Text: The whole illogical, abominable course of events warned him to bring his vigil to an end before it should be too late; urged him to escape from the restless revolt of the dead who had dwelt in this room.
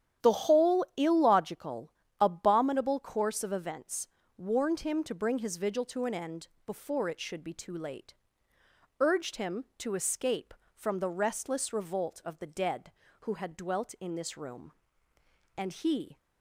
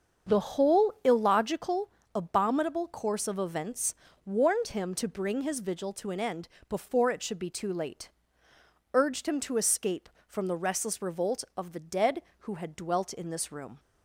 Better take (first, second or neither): second